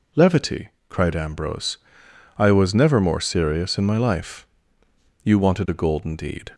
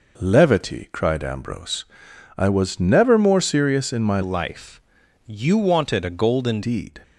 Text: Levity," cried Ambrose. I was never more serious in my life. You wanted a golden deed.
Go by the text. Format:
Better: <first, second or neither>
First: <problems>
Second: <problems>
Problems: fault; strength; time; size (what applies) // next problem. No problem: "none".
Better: first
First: none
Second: changes voice from "life" to "golden"; from 4.2 to 6.6 s; 2.4 s long